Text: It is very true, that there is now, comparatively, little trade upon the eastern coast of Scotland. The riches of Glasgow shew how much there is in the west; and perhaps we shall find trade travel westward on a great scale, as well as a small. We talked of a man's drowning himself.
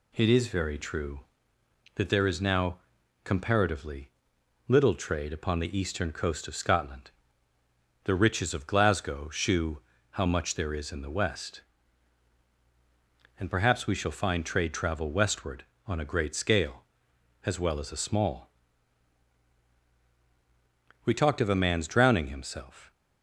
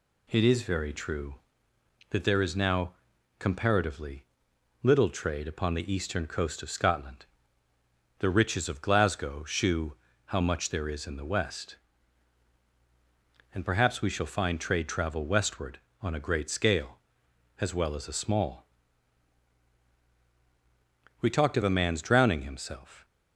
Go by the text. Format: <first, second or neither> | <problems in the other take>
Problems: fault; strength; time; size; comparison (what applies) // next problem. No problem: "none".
neither | pauses between "shew" and "how"; slight; the same in both